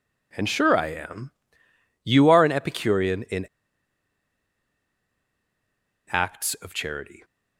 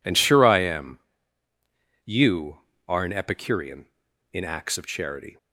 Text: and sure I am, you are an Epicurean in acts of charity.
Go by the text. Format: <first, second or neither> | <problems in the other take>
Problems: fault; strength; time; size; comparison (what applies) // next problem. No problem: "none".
second | pauses between "in" and "acts"; strong; at 3.4 s; 2.6 s long